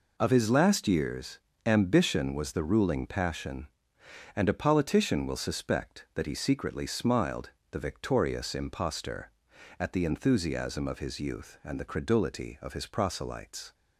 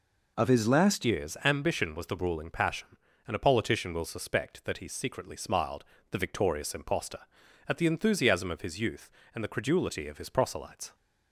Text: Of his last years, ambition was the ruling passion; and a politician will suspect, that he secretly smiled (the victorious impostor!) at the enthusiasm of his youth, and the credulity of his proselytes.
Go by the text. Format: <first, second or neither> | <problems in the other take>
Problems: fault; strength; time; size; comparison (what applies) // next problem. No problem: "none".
first | changes voice at "years"; from 1.0 s on; 9.9 s long